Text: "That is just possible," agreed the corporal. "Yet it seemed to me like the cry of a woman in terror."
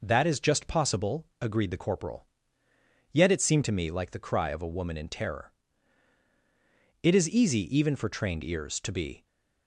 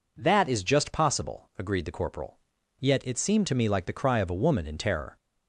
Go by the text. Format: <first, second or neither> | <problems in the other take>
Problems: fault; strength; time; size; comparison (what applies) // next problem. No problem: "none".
second | goes on to say "It is easy even for trained ears to be"; strong; from 7.0 s on; 2.2 s long